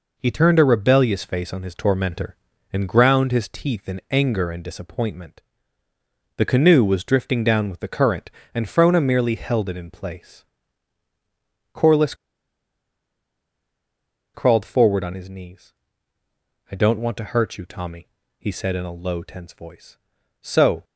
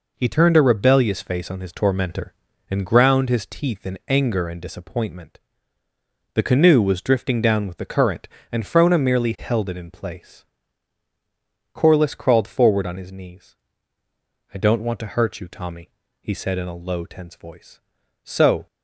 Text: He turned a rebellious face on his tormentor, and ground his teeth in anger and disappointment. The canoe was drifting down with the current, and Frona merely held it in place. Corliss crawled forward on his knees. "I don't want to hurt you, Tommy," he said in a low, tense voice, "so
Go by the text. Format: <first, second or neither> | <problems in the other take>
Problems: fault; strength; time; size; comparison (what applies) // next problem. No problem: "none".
second | pauses between "Corliss" and "crawled"; strong; at 12.1 s; 2.2 s long